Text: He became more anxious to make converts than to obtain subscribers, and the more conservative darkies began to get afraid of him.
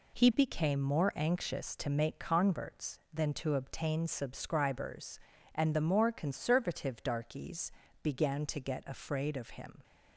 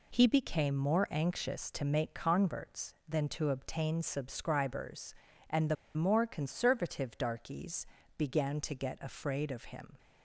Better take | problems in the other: first | pauses between "the" and "more"; slight; at 5.7 s; 0.20 s long // pauses between "darkies" and "began"; slight; at 7.8 s; 0.30 s long; slight in the first

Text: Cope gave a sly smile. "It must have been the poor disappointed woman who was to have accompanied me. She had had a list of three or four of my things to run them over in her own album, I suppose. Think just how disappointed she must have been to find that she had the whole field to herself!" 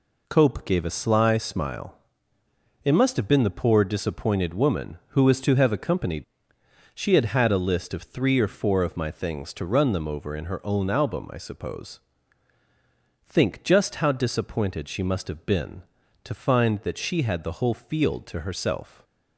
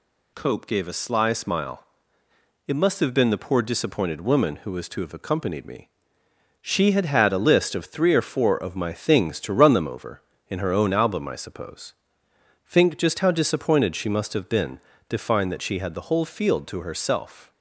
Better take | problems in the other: second | skips "me"; at 6.5 s

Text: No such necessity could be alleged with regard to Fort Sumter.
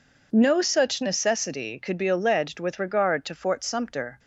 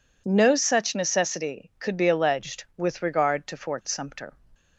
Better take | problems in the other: neither | none

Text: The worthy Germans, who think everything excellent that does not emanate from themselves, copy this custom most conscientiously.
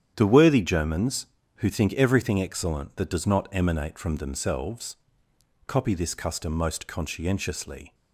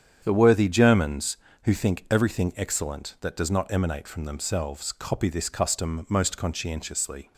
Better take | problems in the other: neither | starts louder than the rest; strong; the same in both

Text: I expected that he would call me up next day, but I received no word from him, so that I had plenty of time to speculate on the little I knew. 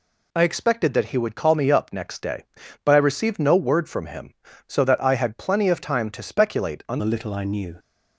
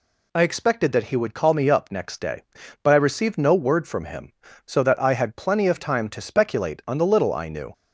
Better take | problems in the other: second | changes voice at "the"; from 6.9 s on; 0.8 s long

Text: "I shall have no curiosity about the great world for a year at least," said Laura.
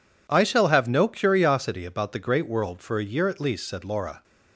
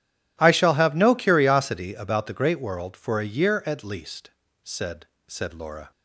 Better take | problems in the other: first | says "said" twice; at 5.2 s

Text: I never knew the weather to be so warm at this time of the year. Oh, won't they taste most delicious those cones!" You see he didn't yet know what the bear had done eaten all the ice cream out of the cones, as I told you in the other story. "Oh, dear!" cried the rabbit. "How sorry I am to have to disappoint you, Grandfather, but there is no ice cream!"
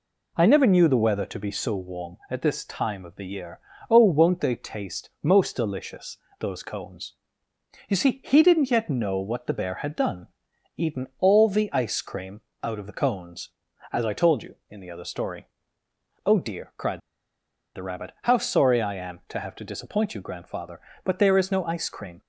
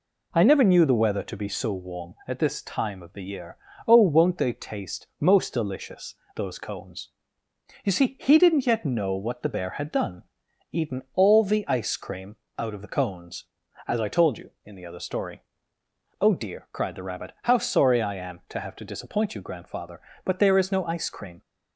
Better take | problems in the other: second | pauses between "delicious" and "those"; slight; at 6.1 s; 0.22 s long; slight in the second // pauses between "done" and "eaten"; noticeable; at 10.2 s; 0.48 s long; noticeable in the second // pauses between "cream" and "out"; slight; at 12.4 s; 0.22 s long; slight in the second // pauses between "cried" and "the"; noticeable; at 16.9 s; 0.75 s long

